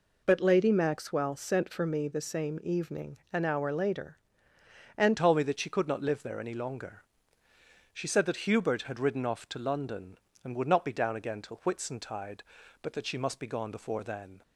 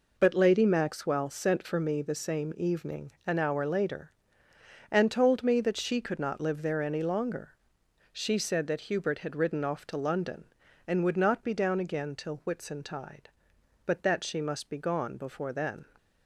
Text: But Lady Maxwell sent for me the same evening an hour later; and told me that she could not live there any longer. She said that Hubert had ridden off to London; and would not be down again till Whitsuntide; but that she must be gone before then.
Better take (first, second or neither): second